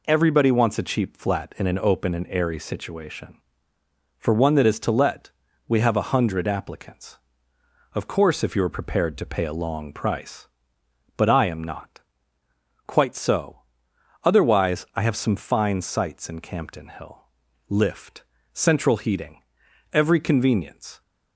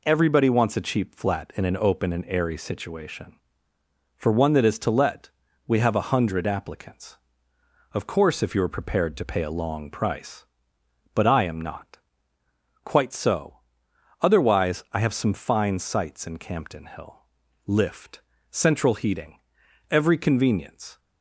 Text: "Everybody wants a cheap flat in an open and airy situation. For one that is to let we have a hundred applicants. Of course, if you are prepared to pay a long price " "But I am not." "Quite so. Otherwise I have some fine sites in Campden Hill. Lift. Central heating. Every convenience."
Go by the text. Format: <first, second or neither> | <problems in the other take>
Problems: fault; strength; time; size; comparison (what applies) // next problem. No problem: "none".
neither | pauses between "let" and "we"; slight; the same in both